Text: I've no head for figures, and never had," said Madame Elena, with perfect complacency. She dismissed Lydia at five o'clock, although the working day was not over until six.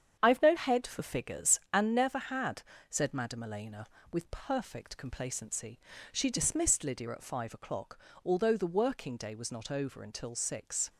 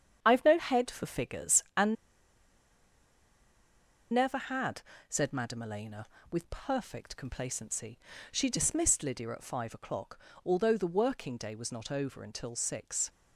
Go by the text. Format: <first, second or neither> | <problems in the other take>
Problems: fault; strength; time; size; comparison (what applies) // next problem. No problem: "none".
first | starts louder than the rest; strong; until 1.2 s; 8.5 dB; strong in the first // pauses between "and" and "never"; strong; at 1.9 s; 2.1 s long